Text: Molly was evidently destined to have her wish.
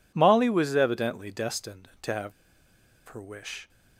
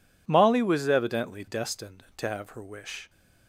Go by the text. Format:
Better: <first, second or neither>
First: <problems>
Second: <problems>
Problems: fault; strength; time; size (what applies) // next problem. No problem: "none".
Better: second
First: pauses between "have" and "her"; noticeable; at 2.3 s; 0.76 s long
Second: none